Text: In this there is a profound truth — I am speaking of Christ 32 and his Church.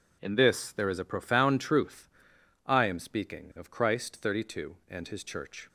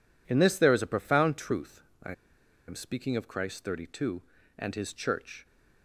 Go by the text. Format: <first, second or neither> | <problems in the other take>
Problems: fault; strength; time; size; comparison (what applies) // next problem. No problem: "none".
first | pauses between "I" and "am"; noticeable; at 2.1 s; 0.55 s long